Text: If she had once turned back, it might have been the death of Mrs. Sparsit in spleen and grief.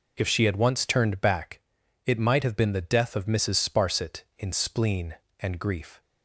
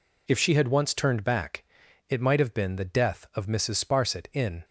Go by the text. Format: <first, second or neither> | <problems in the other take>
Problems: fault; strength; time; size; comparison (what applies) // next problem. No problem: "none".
first | stops before "spleen and grief"; at 4.6 s